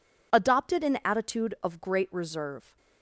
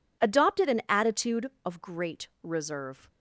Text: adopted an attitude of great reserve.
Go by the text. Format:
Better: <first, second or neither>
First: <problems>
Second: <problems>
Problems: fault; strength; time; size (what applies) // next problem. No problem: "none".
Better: neither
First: none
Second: none